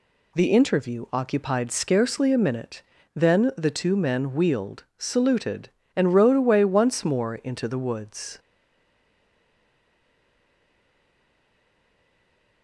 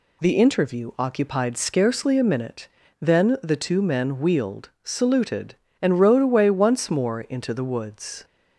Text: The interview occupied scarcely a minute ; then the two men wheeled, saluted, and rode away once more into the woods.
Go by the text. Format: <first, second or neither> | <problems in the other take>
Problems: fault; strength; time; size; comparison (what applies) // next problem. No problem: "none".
second | stays silent after the last word; strong; from 8.3 s on; 4.3 s long